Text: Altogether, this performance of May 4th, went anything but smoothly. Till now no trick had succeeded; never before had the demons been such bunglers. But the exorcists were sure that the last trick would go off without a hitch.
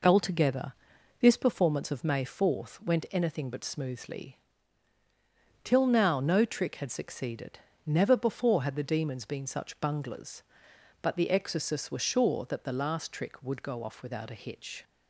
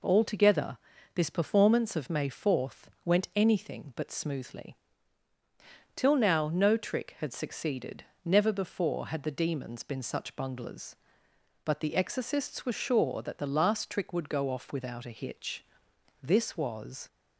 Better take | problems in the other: first | goes on to say "This was"; noticeable; from 16.2 s on; 0.86 s long

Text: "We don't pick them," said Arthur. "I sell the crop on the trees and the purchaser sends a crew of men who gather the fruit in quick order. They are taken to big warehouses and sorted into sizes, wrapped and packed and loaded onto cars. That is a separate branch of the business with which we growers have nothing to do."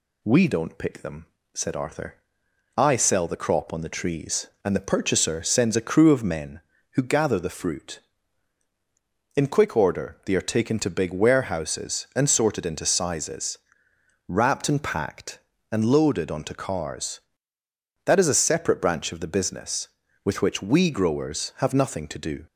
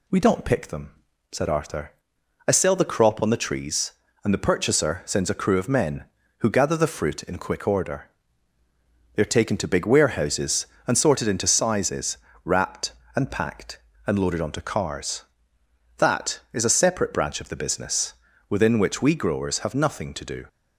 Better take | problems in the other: first | says "within" for "with"; at 18.4 s

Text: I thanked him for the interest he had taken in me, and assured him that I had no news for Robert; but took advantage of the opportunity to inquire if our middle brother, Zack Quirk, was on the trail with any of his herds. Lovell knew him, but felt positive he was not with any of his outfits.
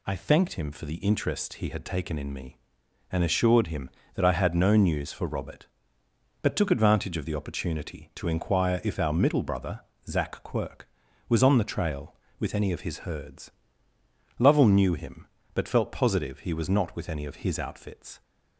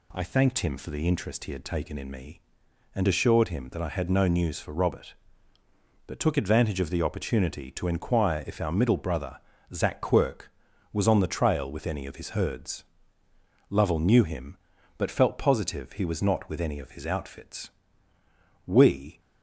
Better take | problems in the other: first | goes on to say "We"; from 18.6 s on; 0.54 s long

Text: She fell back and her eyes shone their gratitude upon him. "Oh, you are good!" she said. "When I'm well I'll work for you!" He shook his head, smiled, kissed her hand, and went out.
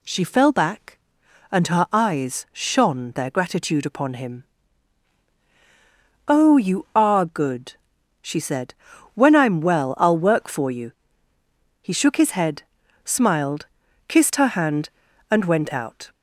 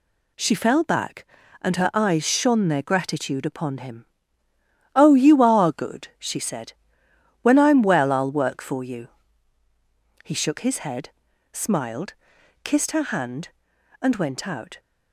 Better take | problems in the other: neither | none

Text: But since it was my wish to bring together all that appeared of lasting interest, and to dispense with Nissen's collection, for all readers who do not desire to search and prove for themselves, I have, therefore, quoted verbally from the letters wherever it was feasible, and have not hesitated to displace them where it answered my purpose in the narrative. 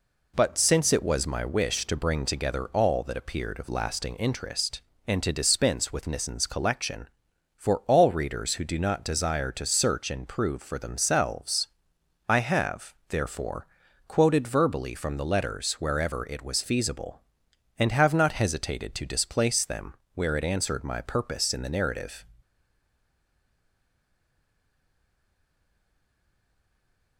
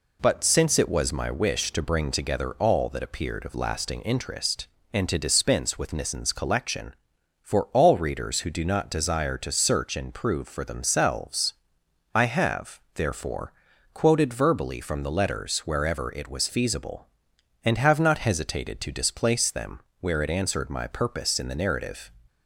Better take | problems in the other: second | pauses between "them" and "where"; slight; at 19.9 s; 0.20 s long; slight in the second // stays silent after the last word; strong; from 22.4 s on; 4.7 s long

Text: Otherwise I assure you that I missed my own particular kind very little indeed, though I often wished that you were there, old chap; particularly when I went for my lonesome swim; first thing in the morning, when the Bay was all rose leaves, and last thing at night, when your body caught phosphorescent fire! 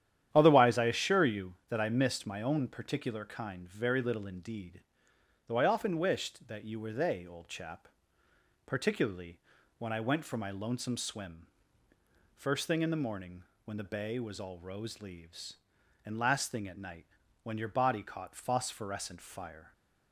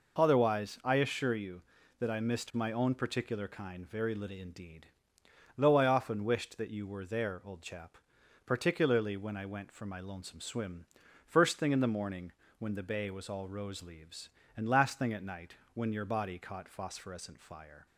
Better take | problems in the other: second | starts louder than the rest; strong; until 1.3 s; 10.5 dB // says "they" for "there"; at 6.9 s // pauses between "particularly" and "when"; at 9.3 s; 0.38 s long

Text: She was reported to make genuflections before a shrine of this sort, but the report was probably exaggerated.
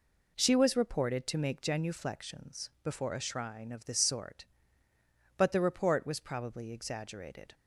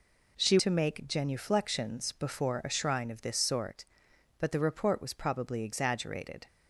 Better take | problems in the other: first | skips "was reported"; at 0.5 s

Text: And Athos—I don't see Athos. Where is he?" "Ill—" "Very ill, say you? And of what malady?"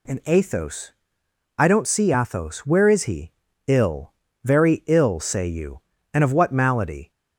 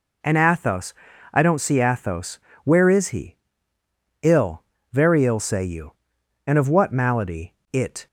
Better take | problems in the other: first | goes on to say "It"; slight; from 7.7 s on; 0.34 s long

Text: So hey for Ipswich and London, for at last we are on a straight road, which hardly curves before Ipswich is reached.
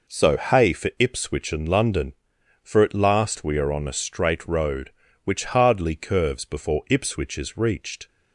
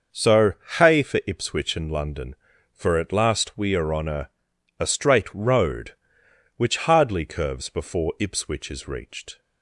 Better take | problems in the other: first | pauses between "So" and "hey"; slight; at 0.5 s; 0.24 s long // says "a" twice; at 4.7 s

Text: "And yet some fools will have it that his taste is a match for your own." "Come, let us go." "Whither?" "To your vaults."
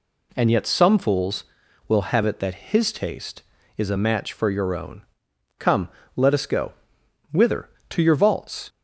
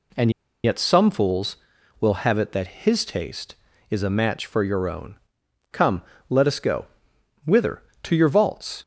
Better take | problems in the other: first | pauses between "And" and "yet"; slight; at 0.3 s; 0.33 s long

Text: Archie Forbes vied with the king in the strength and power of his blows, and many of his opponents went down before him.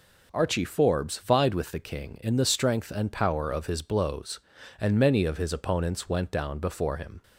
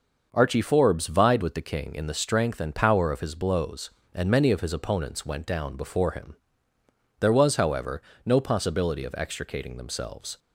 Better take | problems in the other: first | starts louder than the rest; noticeable; until 1.3 s; 6 dB // goes on to say "There was however no possibility of extricating themselves"; strong; from 7.2 s on; 3.1 s long

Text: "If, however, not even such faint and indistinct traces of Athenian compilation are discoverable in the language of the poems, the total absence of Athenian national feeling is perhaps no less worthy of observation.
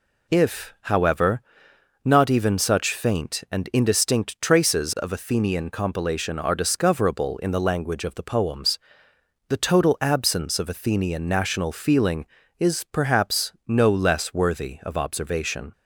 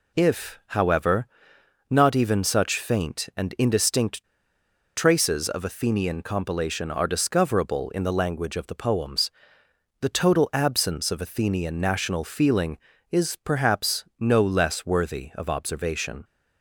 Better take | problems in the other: first | pauses between "indistinct" and "traces"; noticeable; at 4.2 s; 0.71 s long

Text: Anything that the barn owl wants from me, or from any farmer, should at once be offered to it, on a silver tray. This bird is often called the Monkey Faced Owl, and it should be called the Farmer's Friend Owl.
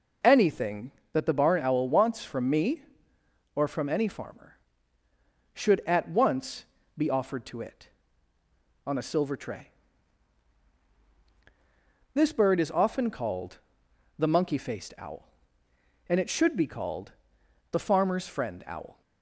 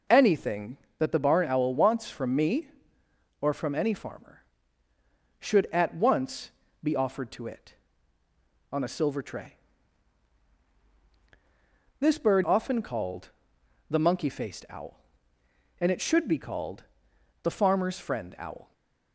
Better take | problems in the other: first | pauses between "once" and "be"; slight; at 6.4 s; 0.32 s long; slight in the first // skips "is"; at 12.4 s // pauses between "called" and "the"; noticeable; at 13.3 s; 0.60 s long; noticeable in the first // pauses between "called" and "the"; noticeable; at 16.8 s; 0.58 s long; noticeable in the first // stays silent after the last word; slight; from 18.6 s on; 0.5 s long

